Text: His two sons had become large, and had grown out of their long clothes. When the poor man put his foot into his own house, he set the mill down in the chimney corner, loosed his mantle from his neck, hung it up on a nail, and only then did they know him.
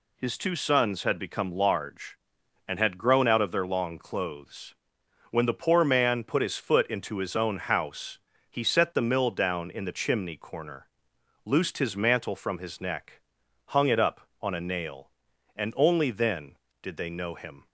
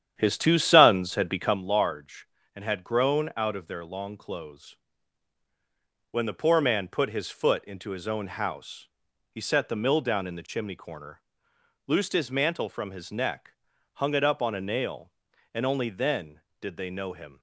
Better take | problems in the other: first | starts louder than the rest; strong; until 1.6 s; 9.5 dB

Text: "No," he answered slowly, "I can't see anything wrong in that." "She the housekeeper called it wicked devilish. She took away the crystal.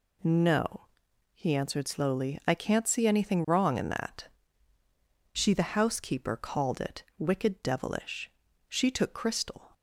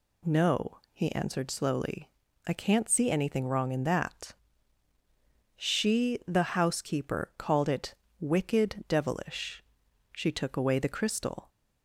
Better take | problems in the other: second | pauses between "it" and "wicked"; slight; at 7.0 s; 0.16 s long; slight in the second // skips "away the"; at 9.1 s

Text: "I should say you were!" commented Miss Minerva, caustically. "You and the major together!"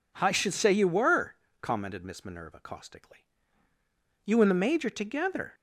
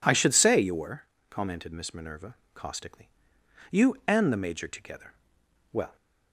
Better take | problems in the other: first | goes on to say "Well"; slight; from 5.7 s on; 0.24 s long

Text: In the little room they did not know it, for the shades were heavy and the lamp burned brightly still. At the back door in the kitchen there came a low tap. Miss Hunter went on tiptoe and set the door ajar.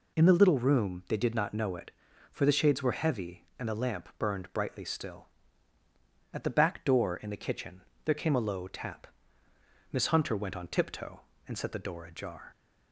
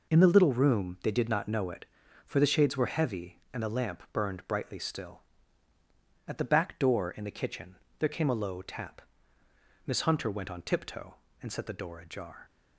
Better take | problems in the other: first | gets quieter; strong; throughout; 8 dB // pauses between "kitchen" and "there"; slight; at 7.7 s; 0.22 s long; slight in the first

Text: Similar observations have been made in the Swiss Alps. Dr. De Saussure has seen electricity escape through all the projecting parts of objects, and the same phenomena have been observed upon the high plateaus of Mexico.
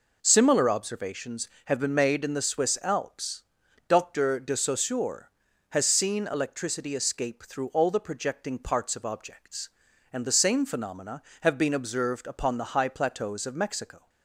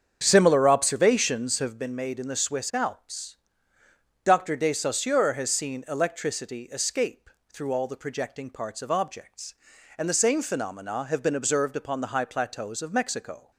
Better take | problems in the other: first | starts louder than the rest; strong; until 1.8 s; 7.5 dB // pauses between "escape" and "through"; slight; at 7.2 s; 0.24 s long

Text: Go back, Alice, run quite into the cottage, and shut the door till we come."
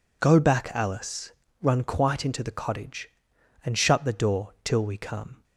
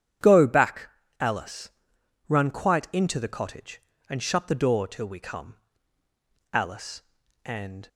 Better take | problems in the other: first | starts louder than the rest; strong; until 1.5 s; 9.5 dB // goes on to say "Alice and"; from 6.5 s on; 1.3 s long

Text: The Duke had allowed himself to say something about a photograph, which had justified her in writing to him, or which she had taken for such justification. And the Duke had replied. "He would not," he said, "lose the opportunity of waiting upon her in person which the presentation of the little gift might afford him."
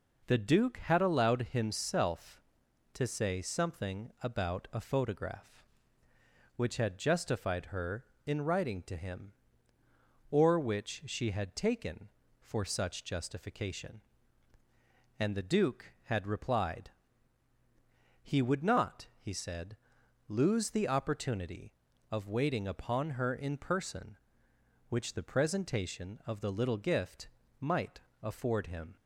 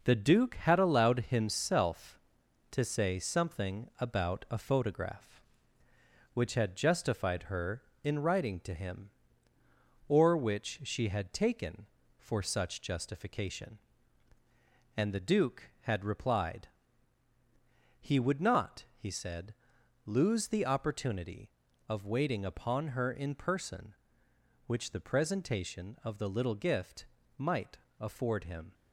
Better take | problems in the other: first | gets quieter; noticeable; throughout; 5.5 dB // pauses between "gift" and "might"; slight; at 27.0 s; 0.32 s long; slight in the first // pauses between "might" and "afford"; slight; at 27.7 s; 0.22 s long; slight in the first

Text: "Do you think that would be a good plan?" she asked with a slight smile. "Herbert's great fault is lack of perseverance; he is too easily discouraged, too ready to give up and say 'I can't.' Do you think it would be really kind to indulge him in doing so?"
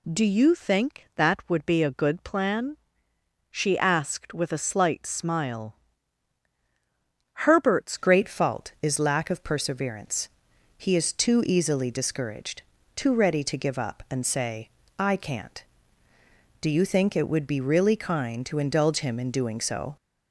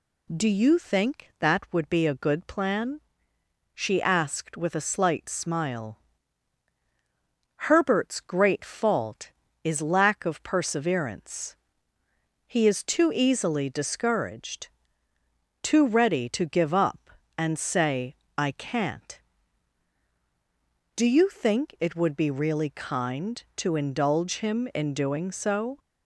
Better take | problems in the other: second | changes voice at "great"; from 7.9 s on; 12.0 s long // pauses between "say" and "I"; slight; at 14.6 s; 0.30 s long; slight in the second

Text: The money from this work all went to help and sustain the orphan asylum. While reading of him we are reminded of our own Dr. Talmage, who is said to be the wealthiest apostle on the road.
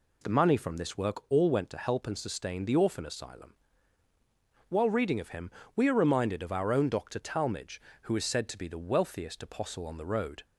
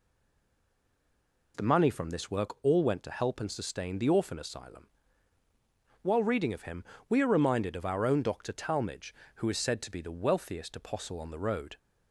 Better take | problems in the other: first | stays silent before the first word; noticeable; until 1.5 s; 1.5 s long // pauses between "him" and "we"; slight; at 6.8 s; 0.24 s long; slight in the first

